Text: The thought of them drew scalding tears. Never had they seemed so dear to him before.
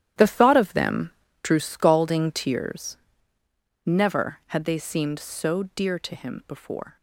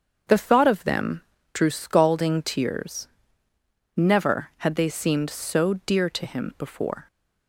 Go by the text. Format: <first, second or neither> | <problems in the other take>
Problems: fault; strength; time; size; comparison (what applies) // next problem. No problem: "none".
second | gets quieter; strong; throughout; 12 dB // starts louder than the rest; strong; until 1.5 s; 11.5 dB; also in the second // pauses between "them" and "drew"; slight; at 1.1 s; 0.32 s long; slight in the second